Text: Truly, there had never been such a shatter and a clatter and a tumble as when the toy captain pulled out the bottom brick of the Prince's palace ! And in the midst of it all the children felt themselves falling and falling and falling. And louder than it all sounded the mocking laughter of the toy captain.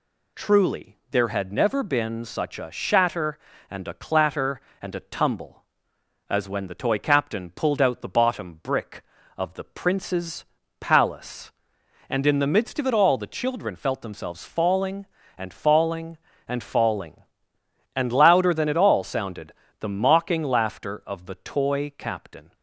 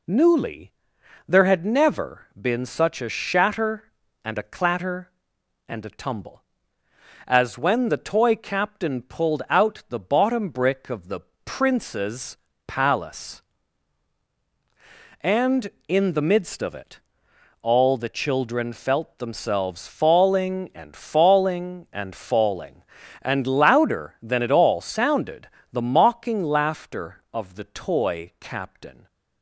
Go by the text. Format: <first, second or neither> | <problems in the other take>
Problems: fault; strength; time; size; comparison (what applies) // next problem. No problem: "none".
first | says "Newly" for "Truly"; at 0.0 s // pauses between "the" and "Prince's"; slight; at 11.2 s; 0.26 s long // pauses between "Prince's" and "palace"; slight; at 12.3 s; 0.30 s long; slight in the first // pauses between "it" and "all"; noticeable; at 17.0 s; 0.62 s long // pauses between "sounded" and "the"; slight; at 25.4 s; 0.24 s long; slight in the first